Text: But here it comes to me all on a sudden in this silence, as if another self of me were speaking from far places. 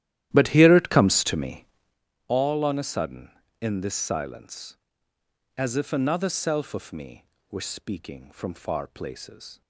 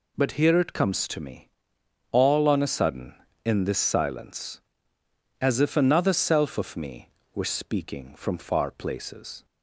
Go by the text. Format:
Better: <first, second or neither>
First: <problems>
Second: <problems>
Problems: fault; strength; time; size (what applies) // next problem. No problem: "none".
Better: second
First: starts louder than the rest; strong; until 2.0 s; 13 dB // pauses between "me" and "all"; noticeable; at 1.6 s; 0.62 s long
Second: pauses between "me" and "all"; noticeable; at 1.4 s; 0.62 s long